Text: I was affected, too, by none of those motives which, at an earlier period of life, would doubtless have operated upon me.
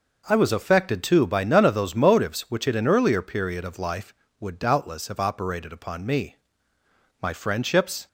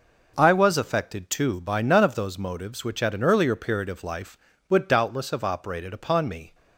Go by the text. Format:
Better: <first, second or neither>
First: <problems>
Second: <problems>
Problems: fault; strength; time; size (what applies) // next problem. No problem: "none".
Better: second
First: goes on to say "My friendships"; noticeable; from 7.2 s on; 0.86 s long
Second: none